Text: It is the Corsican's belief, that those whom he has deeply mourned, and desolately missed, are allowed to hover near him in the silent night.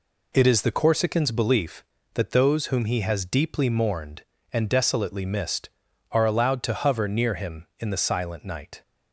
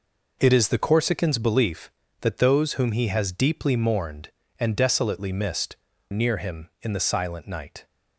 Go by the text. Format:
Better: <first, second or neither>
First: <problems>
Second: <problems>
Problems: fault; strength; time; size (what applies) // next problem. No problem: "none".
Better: first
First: none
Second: skips "are allowed to hover"; at 5.9 s